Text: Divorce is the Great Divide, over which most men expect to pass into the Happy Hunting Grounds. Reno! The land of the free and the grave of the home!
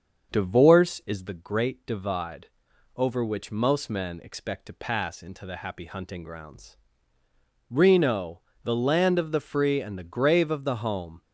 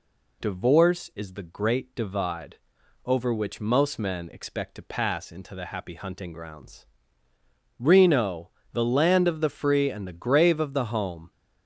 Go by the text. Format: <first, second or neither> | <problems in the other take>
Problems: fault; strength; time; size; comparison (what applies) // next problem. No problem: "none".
second | starts louder than the rest; until 1.5 s; 6.5 dB